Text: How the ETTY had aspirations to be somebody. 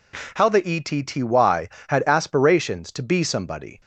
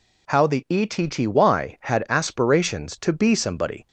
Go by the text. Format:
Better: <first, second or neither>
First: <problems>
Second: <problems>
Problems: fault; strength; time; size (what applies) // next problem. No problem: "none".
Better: neither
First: none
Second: none